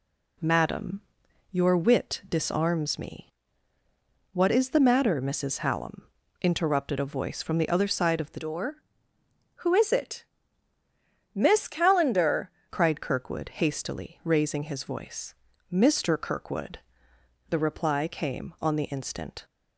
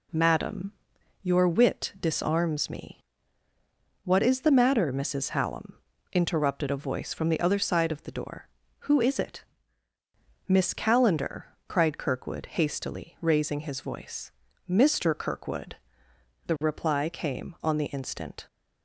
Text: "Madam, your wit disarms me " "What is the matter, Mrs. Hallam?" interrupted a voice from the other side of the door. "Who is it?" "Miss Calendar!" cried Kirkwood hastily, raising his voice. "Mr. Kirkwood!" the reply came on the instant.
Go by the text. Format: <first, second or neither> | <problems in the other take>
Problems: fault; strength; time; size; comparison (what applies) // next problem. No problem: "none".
second | changes voice from "door" to "Calendar"; from 8.3 to 12.4 s; 4.1 s long